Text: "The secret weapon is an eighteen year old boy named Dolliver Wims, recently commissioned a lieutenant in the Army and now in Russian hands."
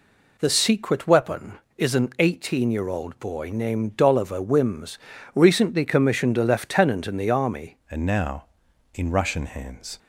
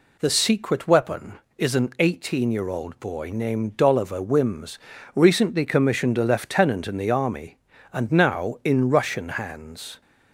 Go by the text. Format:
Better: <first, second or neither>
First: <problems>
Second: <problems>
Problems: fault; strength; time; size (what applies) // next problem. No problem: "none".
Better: second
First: changes voice at "and"; from 7.8 s on; 2.1 s long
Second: none